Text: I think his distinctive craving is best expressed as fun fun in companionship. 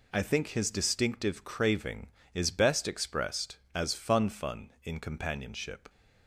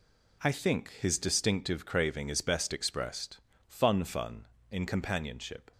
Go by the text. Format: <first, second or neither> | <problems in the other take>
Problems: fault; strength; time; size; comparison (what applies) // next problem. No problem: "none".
first | skips "as"; at 3.5 s